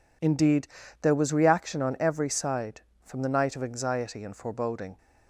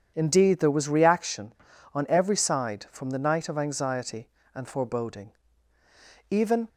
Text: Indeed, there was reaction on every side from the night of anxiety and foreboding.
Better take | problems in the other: first | goes on to say "Even"; slight; from 6.2 s on; 0.38 s long

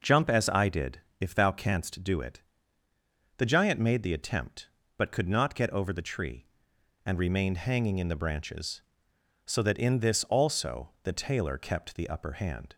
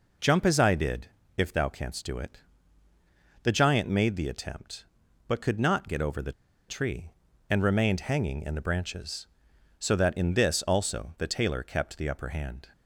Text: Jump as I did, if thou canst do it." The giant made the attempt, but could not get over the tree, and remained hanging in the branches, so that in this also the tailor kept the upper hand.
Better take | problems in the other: first | pauses between "the" and "tree"; at 6.3 s; 0.37 s long

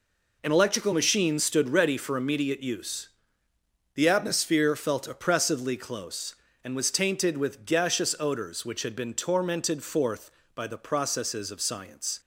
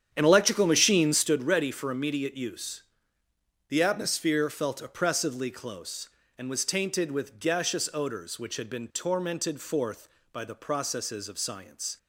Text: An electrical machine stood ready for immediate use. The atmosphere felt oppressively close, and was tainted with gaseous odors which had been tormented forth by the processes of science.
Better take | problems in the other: first | starts louder than the rest; strong; until 1.3 s; 9 dB

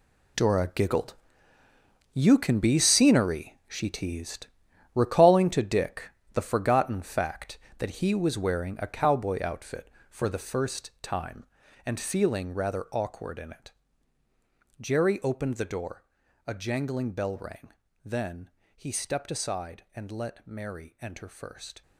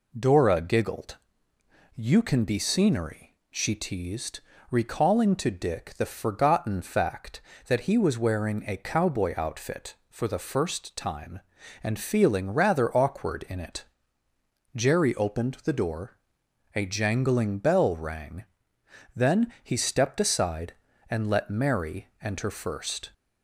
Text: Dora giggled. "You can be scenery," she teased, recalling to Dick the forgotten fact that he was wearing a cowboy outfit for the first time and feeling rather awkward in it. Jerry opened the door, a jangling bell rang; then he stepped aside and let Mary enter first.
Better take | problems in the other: second | gets quieter; strong; throughout; 13.5 dB // pauses between "Dick" and "the"; slight; at 6.0 s; 0.24 s long // pauses between "then" and "he"; slight; at 18.4 s; 0.26 s long

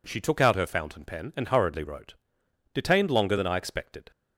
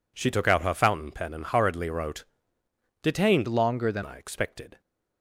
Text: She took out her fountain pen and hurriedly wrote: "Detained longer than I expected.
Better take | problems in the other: first | changes voice from "longer" to "than"; from 3.4 to 4.0 s; 0.6 s long

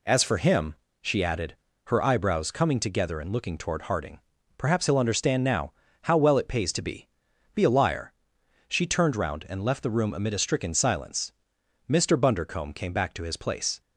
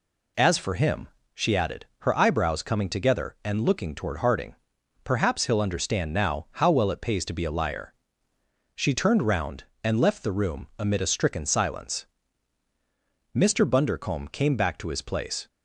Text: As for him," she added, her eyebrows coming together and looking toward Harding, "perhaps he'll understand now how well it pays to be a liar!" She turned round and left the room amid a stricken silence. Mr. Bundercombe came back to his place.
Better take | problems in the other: second | pauses between "now" and "how"; slight; at 5.7 s; 0.30 s long // says "be" twice; at 7.5 s

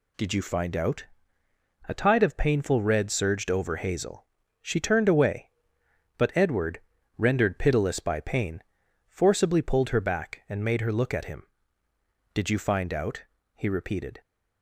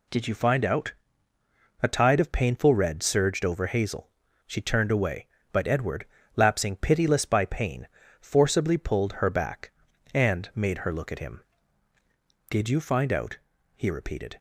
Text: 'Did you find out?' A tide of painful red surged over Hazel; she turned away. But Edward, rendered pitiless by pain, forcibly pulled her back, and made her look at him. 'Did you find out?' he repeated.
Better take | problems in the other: first | says "lapsing" for "rendered"; at 6.3 s

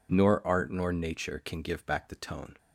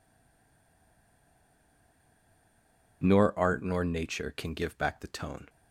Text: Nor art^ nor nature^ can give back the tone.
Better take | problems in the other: first | stays silent before the first word; strong; until 3.0 s; 3.0 s long

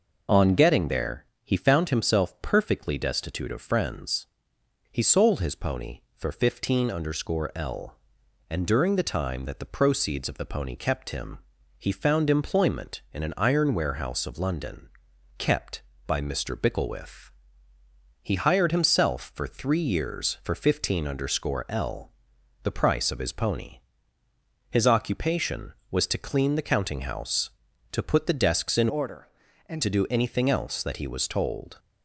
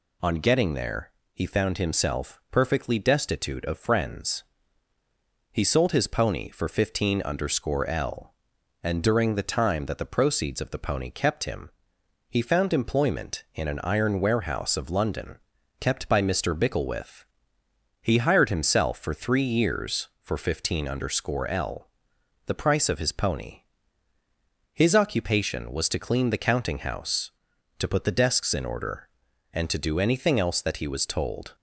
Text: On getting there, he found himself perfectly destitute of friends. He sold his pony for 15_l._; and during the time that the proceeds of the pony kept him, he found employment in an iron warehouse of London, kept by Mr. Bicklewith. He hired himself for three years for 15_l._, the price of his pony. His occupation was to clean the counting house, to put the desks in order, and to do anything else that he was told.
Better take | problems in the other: second | changes voice from "order" to "and"; from 28.8 to 29.8 s; 1.0 s long

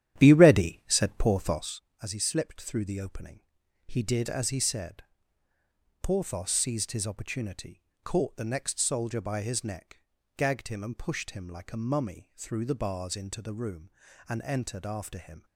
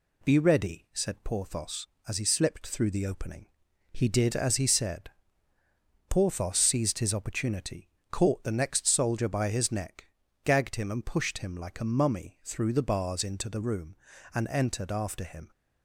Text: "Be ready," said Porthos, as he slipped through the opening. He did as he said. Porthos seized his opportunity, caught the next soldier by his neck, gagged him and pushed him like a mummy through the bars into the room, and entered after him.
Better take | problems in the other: second | starts louder than the rest; strong; until 1.8 s; 10.5 dB

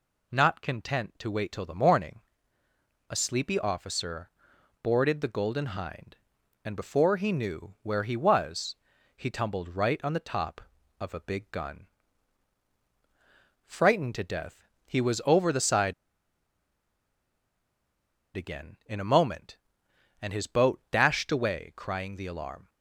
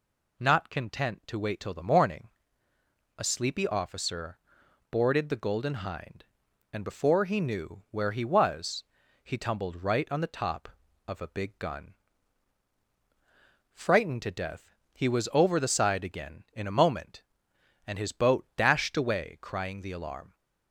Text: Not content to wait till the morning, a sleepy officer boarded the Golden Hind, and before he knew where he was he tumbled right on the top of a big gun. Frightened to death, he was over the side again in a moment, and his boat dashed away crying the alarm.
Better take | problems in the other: second | pauses between "officer" and "boarded"; noticeable; at 4.2 s; 0.54 s long; noticeable in the second // pauses between "was" and "he"; at 8.7 s; 0.42 s long; also in the second // pauses between "side" and "again"; strong; at 15.9 s; 2.4 s long

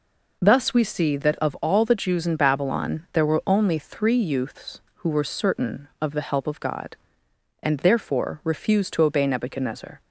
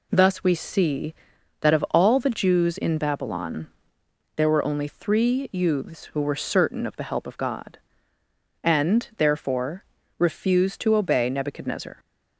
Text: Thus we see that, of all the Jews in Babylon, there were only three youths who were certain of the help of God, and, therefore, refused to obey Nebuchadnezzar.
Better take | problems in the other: neither | none

